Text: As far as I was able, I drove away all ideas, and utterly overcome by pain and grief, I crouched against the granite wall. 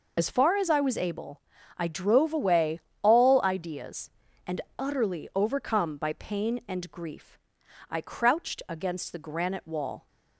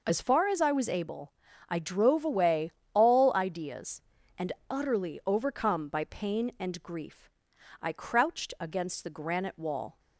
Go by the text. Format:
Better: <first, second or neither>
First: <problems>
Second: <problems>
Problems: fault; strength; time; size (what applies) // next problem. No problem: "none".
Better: second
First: loses the start of "As"; at 0.1 s; 45 ms // pauses between "away" and "all"; slight; at 2.8 s; 0.20 s long // pauses between "and" and "utterly"; slight; at 4.5 s; 0.18 s long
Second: pauses between "away" and "all"; slight; at 2.7 s; 0.20 s long // pauses between "and" and "utterly"; slight; at 4.5 s; 0.18 s long